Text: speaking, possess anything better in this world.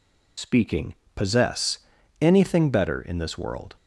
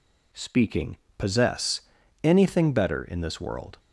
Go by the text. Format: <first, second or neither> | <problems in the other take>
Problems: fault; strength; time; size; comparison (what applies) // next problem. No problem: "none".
second | loses the start of "speaking"; at 0.3 s; 75 ms // pauses between "possess" and "anything"; at 1.7 s; 0.42 s long; also in the second